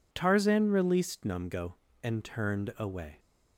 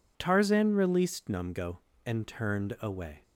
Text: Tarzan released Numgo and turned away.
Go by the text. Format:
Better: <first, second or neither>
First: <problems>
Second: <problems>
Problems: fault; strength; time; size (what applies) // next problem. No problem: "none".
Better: neither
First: none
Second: none